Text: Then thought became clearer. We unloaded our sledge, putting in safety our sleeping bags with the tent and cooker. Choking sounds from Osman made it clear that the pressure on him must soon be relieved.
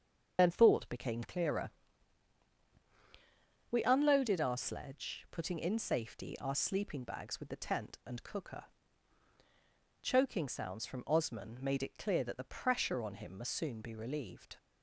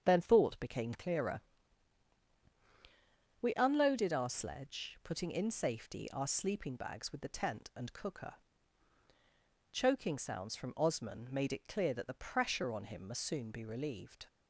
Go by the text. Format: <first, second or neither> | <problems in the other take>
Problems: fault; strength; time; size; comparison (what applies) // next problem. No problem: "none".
second | loses the start of "Then"; at 0.3 s; 45 ms // starts louder than the rest; until 1.3 s; 7 dB; strong in the second